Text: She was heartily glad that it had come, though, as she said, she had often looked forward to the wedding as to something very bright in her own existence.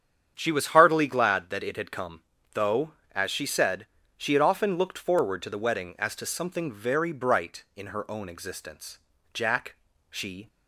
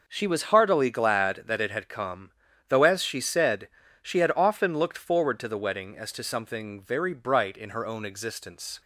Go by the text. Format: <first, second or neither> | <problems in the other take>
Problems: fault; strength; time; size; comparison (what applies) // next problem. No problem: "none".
second | starts louder than the rest; strong; until 1.3 s; 8.5 dB // goes on to say "Jack she"; noticeable; from 9.3 s on; 1.1 s long